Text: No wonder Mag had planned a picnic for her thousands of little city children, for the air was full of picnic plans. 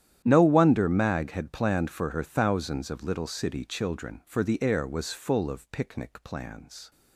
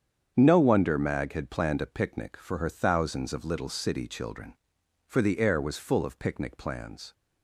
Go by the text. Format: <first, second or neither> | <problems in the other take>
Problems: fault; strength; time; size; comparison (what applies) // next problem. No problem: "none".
second | starts louder than the rest; strong; until 1.2 s; 10.5 dB; strong in the second // skips "a picnic"; at 1.9 s